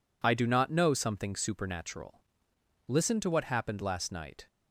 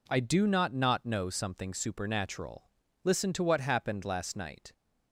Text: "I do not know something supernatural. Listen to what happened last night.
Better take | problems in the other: first | says "not" twice; at 0.7 s

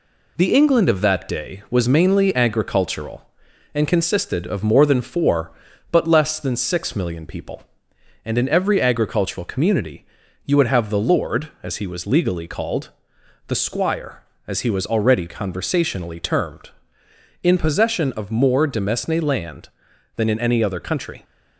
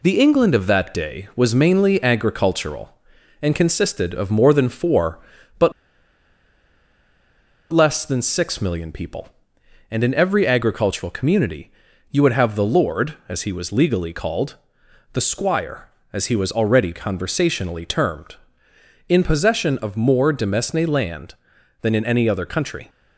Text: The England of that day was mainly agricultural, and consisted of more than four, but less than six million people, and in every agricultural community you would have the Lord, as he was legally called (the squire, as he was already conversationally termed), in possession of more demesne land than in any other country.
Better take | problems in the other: first | pauses between "but" and "less"; strong; at 5.7 s; 2.0 s long // pauses between "community" and "you"; at 11.7 s; 0.40 s long; also in the first

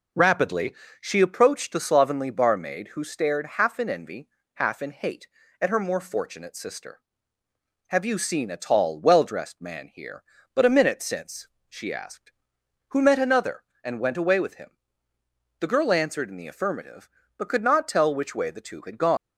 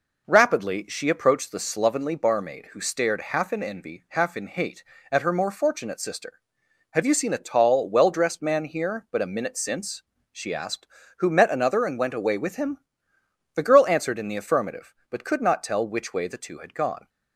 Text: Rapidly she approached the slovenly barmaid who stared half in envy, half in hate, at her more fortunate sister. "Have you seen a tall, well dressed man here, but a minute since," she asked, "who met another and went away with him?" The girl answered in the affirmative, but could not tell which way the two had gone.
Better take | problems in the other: second | pauses between "Rapidly" and "she"; slight; at 0.7 s; 0.26 s long // leaves "gone" unfinished; at 19.1 s; 155 ms

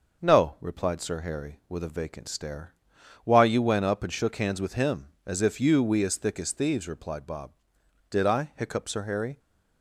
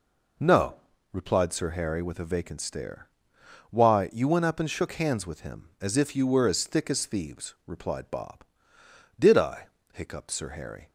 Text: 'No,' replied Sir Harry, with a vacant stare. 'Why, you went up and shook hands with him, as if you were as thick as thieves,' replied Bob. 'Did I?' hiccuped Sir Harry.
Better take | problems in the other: second | says "we" for "were"; at 5.8 s

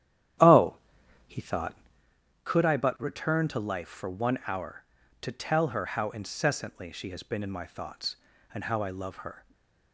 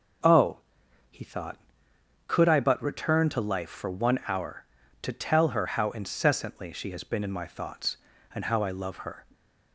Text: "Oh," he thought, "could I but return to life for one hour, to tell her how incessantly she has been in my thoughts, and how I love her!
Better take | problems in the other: second | starts louder than the rest; strong; until 2.2 s; 11 dB // stays silent after the last word; slight; from 9.3 s on; 0.6 s long

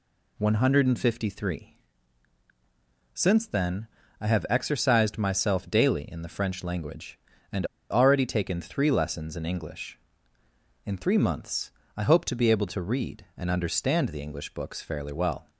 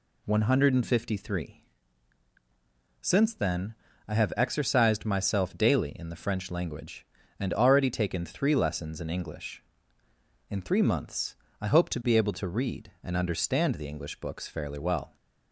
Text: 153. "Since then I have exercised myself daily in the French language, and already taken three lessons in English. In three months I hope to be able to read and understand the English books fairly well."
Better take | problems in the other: second | pauses between "then" and "I"; slight; at 3.8 s; 0.32 s long; slight in the second // pauses between "and" and "already"; slight; at 7.6 s; 0.24 s long // pauses between "months" and "I"; slight; at 11.7 s; 0.24 s long; slight in the second

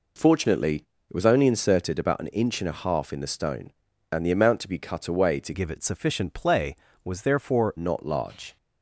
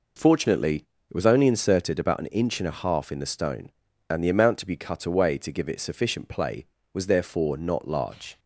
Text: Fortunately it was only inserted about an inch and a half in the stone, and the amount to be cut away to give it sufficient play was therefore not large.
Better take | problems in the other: second | pauses between "Fortunately" and "it"; slight; at 0.7 s; 0.34 s long; slight in the second // changes voice from "give" to "therefore"; from 5.5 to 7.7 s; 2.2 s long

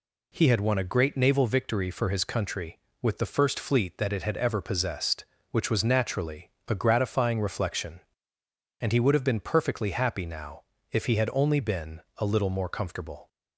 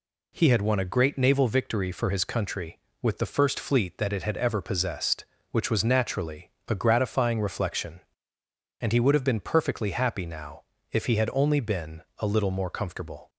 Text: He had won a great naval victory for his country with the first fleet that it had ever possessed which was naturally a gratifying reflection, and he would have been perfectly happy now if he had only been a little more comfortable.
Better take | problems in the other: neither | pauses between "naturally" and "a"; slight; the same in both // pauses between "now" and "if"; slight; the same in both // pauses between "been" and "a"; slight; the same in both

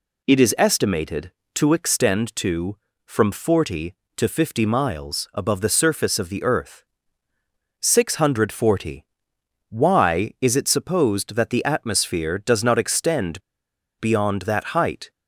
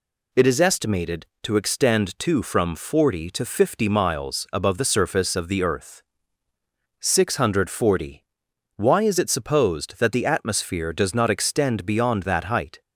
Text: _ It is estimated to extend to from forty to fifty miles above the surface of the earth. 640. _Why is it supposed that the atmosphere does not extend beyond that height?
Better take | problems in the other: second | pauses between "extend" and "beyond"; noticeable; at 13.4 s; 0.59 s long

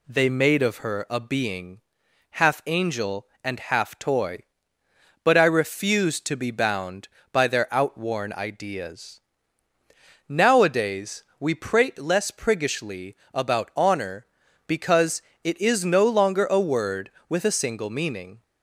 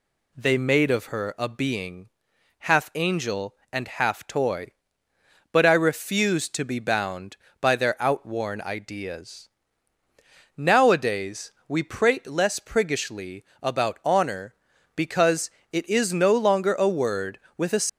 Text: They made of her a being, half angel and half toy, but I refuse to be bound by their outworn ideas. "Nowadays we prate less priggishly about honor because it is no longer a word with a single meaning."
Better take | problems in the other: first | pauses between "Nowadays" and "we"; slight; at 11.5 s; 0.18 s long; slight in the first // pauses between "priggishly" and "about"; slight; at 13.4 s; 0.16 s long; slight in the first // pauses between "because" and "it"; slight; at 15.5 s; 0.20 s long; slight in the first // stops before "single meaning"; at 17.8 s

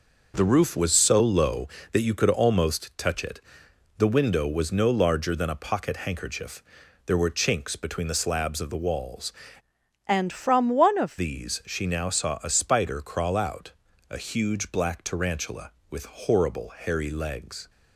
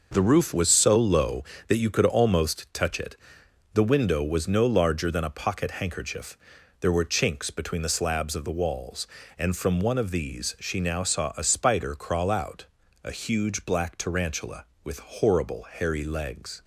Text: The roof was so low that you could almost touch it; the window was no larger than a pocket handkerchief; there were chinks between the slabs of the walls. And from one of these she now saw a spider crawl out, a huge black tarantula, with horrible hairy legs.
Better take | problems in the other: second | changes voice from "And" to "of"; from 10.0 to 11.1 s; 1.1 s long

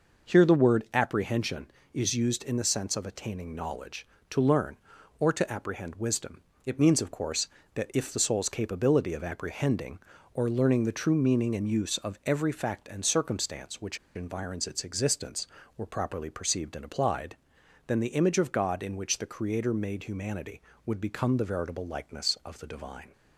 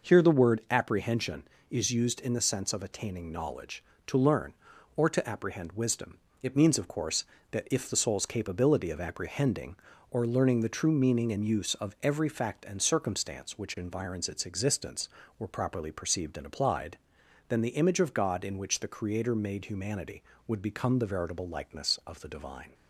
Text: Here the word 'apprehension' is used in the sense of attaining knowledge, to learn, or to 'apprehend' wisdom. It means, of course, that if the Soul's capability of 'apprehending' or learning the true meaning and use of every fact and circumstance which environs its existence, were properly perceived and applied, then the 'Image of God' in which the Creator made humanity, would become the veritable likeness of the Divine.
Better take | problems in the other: second | pauses between "which" and "environs"; slight; at 13.9 s; 0.20 s long

